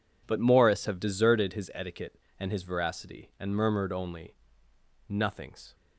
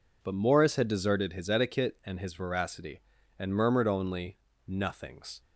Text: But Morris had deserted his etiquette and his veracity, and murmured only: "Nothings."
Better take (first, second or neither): second